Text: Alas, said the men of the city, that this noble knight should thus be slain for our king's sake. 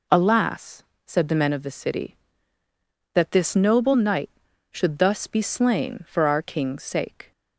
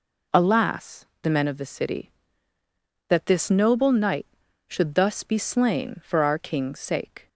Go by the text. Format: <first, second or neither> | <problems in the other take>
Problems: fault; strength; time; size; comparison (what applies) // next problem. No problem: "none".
first | skips "said"; at 1.1 s